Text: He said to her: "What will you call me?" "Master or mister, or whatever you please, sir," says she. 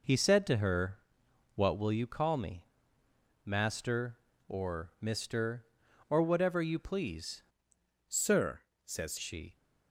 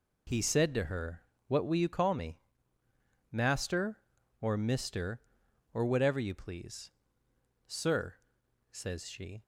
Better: second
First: changes voice from "sir" to "says"; from 8.1 to 9.1 s; 1.0 s long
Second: none

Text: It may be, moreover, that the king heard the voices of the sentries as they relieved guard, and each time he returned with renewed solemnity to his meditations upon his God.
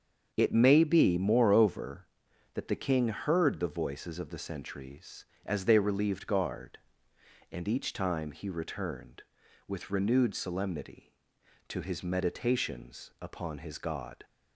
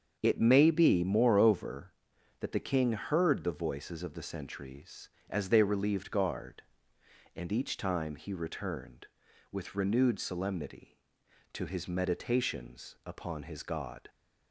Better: neither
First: starts louder than the rest; until 1.3 s; 7 dB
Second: starts louder than the rest; until 1.2 s; 7 dB

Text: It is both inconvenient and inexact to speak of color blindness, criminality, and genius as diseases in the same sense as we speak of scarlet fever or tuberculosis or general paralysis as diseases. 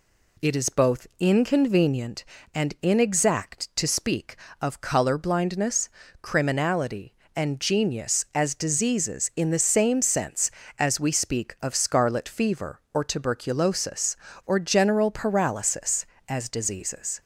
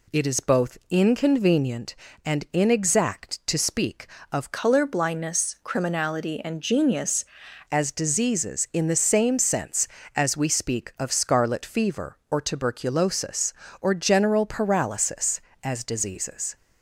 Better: first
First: none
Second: changes voice from "color" to "genius"; from 4.5 to 7.2 s; 2.7 s long

